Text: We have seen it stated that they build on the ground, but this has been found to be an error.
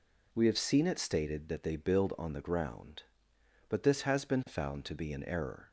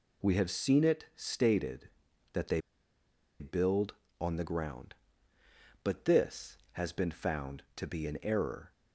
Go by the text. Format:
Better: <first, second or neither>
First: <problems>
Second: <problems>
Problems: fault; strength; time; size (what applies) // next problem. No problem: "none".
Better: first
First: none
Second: pauses between "they" and "build"; noticeable; at 2.6 s; 0.79 s long